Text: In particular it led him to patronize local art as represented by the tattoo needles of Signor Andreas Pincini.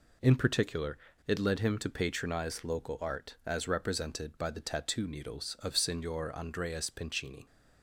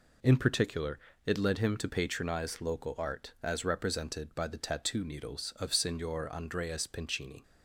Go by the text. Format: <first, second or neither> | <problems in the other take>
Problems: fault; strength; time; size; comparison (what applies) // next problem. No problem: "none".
neither | pauses between "particular" and "it"; slight; the same in both